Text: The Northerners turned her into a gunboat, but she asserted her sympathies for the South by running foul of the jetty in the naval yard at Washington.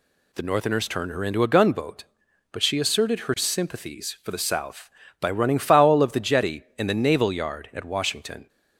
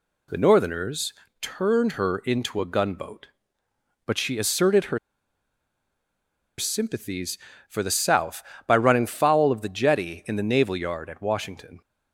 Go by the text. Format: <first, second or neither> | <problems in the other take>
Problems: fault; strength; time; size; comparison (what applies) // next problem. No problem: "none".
first | pauses between "Northerners" and "turned"; slight; at 1.1 s; 0.30 s long // pauses between "her" and "sympathies"; strong; at 4.9 s; 1.6 s long